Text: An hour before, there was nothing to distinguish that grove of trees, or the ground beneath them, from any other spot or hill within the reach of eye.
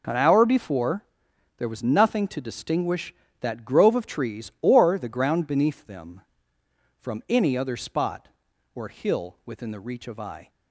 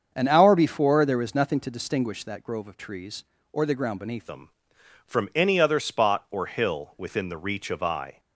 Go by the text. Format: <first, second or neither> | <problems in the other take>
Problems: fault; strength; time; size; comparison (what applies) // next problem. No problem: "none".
first | starts louder than the rest; until 1.1 s; 7 dB // changes voice at "them"; from 4.2 s on; 3.9 s long